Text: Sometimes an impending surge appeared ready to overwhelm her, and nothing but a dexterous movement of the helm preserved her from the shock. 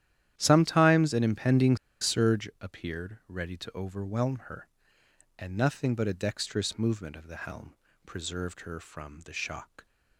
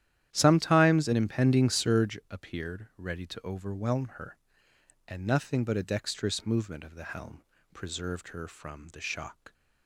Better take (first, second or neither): second